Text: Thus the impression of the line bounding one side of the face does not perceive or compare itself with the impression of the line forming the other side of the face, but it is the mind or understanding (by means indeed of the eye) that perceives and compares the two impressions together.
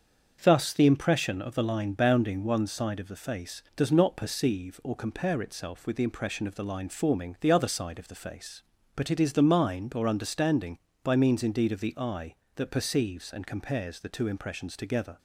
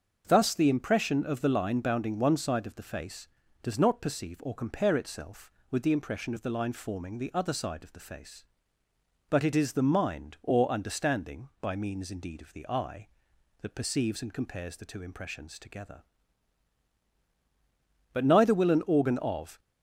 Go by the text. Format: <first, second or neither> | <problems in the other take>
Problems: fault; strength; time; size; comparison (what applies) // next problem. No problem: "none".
first | starts louder than the rest; until 1.2 s; 6.5 dB; also in the first // goes on to say "But neither will an organ of"; from 18.1 s on; 1.4 s long